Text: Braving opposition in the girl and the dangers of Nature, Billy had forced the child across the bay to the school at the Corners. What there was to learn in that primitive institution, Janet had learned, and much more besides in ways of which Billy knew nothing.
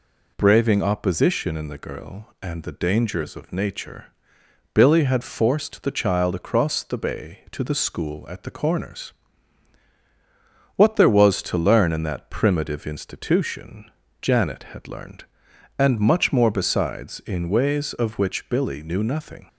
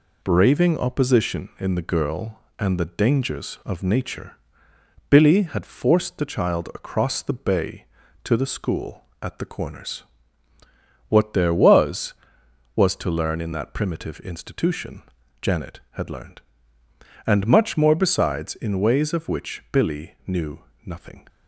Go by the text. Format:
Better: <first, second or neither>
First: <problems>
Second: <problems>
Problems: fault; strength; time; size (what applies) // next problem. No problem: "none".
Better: first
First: none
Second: says "was" twice; at 12.7 s // pauses between "knew" and "nothing"; slight; at 20.5 s; 0.26 s long